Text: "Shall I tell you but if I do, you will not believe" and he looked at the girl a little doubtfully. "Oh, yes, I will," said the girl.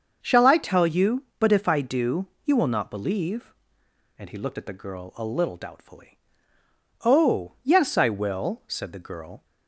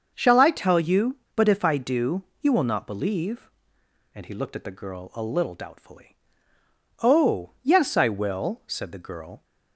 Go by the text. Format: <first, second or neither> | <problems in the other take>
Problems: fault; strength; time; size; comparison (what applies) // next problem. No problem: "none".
neither | starts louder than the rest; the same in both